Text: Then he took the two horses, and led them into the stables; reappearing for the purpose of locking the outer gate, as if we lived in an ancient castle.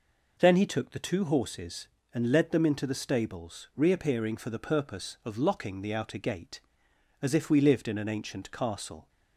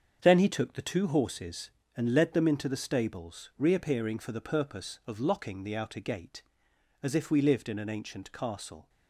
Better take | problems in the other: first | gets quieter; strong; throughout; 8 dB

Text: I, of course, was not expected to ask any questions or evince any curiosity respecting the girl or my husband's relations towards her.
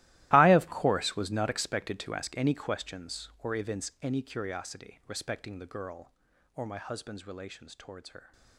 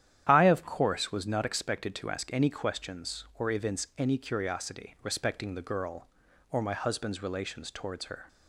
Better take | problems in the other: second | gets quieter; strong; throughout; 17 dB // starts louder than the rest; strong; until 1.3 s; 16.5 dB; strong in the second

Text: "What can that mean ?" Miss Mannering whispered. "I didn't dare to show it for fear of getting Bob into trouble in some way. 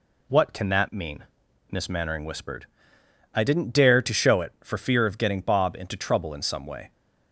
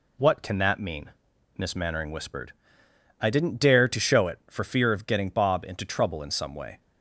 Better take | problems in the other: neither | none

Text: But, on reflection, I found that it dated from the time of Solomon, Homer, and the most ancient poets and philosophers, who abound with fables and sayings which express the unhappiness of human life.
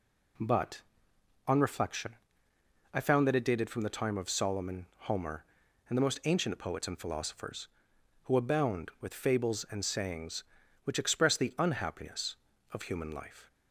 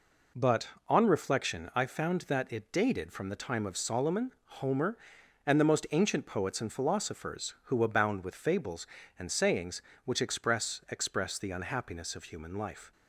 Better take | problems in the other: first | says "express" twice; at 10.8 s

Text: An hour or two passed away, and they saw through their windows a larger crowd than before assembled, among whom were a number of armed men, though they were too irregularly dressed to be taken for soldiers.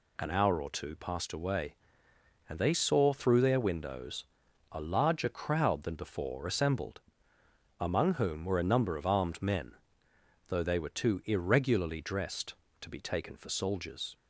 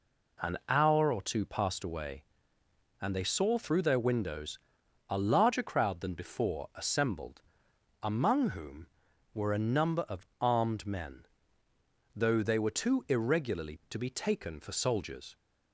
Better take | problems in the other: first | pauses between "windows" and "a"; noticeable; at 4.5 s; 0.52 s long; noticeable in the first // pauses between "of" and "armed"; slight; at 10.2 s; 0.16 s long // skips "dressed"; at 13.8 s

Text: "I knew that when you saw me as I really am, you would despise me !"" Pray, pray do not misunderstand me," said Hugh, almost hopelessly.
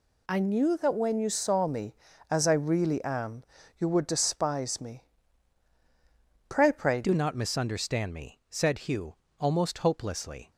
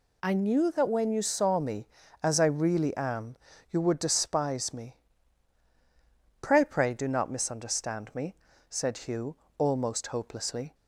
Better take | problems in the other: second | changes voice at "do"; from 7.0 s on; 3.5 s long

